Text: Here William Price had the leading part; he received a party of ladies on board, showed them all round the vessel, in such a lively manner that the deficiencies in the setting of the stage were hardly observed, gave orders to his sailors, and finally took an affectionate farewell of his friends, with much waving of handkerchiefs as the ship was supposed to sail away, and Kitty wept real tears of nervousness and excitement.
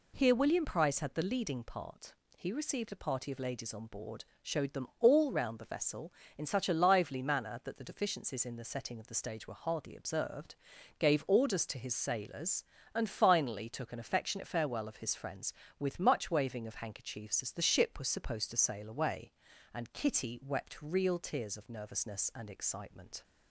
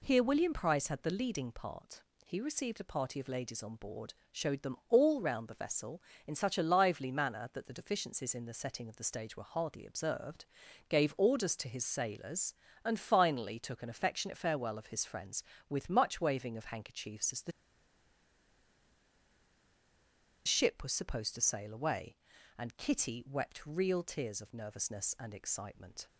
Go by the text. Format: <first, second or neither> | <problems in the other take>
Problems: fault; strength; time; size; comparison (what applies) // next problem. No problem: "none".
first | pauses between "the" and "ship"; strong; at 17.5 s; 2.9 s long